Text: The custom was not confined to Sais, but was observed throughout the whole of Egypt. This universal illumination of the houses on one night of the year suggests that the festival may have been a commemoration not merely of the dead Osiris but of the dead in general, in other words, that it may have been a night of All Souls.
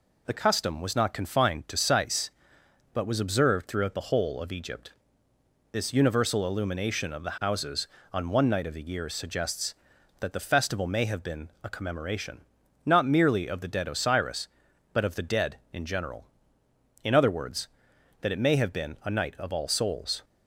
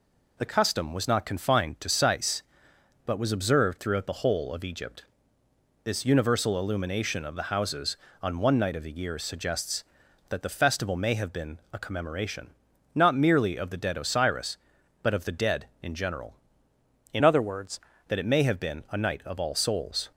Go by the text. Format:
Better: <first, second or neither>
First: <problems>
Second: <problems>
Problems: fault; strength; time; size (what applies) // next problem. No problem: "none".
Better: first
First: pauses between "commemoration" and "not"; noticeable; at 12.3 s; 0.46 s long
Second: pauses between "commemoration" and "not"; noticeable; at 12.4 s; 0.46 s long // changes voice from "other" to "words"; from 17.2 to 17.7 s; 0.5 s long